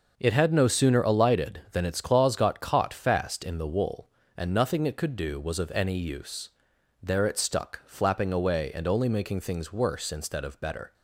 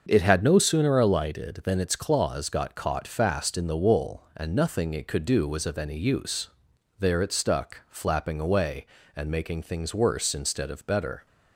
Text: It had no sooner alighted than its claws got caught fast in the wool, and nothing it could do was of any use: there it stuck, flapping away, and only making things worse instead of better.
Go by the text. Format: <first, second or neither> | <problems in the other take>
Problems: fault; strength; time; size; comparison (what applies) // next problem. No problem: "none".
first | starts louder than the rest; until 1.0 s; 6.5 dB // skips "only"; at 9.2 s